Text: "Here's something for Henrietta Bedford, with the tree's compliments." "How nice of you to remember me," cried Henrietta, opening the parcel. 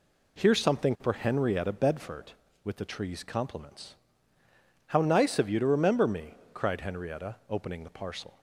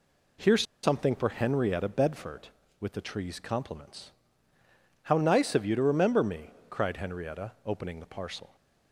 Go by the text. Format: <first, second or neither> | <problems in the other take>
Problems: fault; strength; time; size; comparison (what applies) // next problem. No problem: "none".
first | pauses between "Here's" and "something"; slight; at 0.6 s; 0.19 s long